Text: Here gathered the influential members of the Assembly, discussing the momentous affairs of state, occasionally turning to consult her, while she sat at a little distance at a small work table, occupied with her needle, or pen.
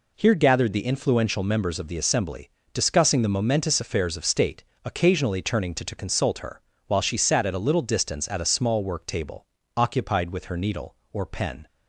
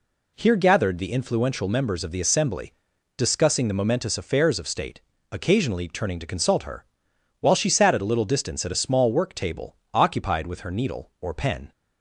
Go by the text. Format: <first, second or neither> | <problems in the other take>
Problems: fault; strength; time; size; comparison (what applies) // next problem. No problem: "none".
second | says "to" twice; at 5.8 s